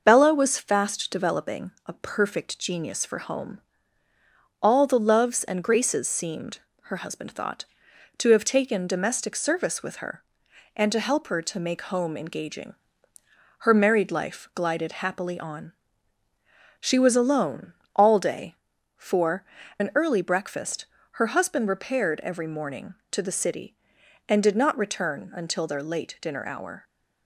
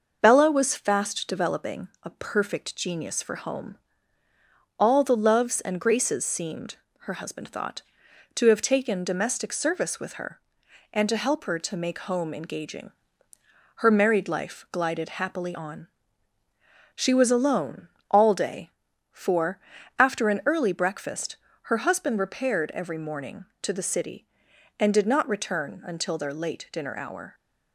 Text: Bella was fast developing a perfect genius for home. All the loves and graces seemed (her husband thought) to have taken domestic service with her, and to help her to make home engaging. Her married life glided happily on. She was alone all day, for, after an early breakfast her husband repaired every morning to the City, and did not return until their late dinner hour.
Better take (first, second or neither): second